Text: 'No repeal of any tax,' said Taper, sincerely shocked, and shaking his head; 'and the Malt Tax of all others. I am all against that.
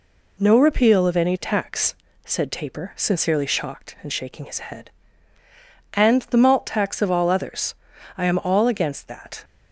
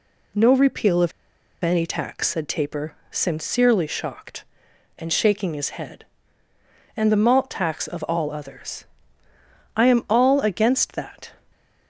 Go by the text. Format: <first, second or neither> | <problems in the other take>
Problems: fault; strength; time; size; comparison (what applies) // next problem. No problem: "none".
first | pauses between "of" and "any"; noticeable; at 1.1 s; 0.51 s long